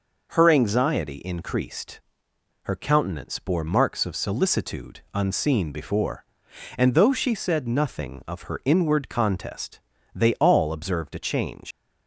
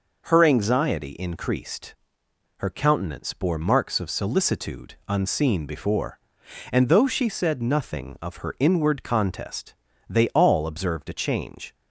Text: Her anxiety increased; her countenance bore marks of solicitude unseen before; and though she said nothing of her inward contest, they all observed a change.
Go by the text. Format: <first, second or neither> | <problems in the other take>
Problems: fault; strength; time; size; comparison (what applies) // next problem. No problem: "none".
second | leaves "change" unfinished; at 11.7 s; 90 ms